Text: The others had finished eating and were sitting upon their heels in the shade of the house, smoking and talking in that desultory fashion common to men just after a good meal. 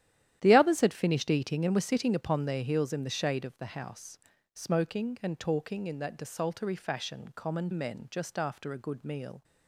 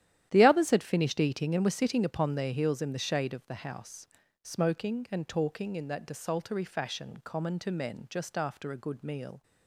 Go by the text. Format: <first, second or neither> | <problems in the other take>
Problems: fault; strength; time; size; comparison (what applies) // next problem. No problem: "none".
second | starts louder than the rest; strong; until 1.4 s; 11.5 dB; strong in the second // skips "to"; at 7.7 s